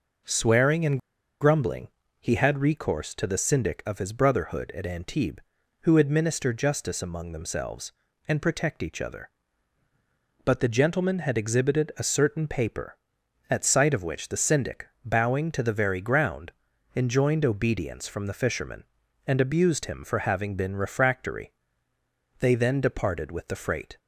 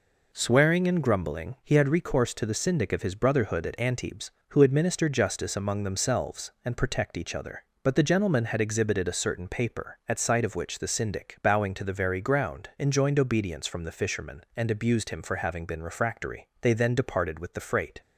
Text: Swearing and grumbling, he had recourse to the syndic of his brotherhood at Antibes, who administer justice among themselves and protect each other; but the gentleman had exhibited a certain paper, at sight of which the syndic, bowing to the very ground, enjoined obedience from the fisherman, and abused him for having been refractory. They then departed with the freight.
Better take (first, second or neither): second